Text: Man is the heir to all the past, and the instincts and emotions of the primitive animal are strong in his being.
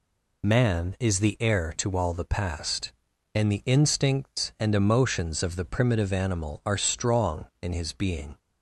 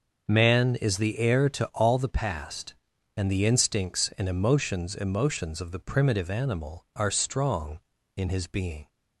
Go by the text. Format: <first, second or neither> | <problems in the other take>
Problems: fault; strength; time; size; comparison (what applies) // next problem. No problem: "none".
first | starts louder than the rest; noticeable; until 1.2 s; 6 dB // says "emotions" twice; at 4.9 s